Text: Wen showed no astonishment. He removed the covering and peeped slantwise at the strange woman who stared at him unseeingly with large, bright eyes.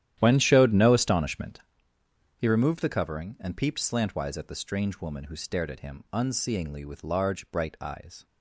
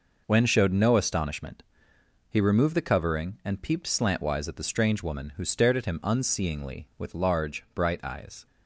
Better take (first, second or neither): second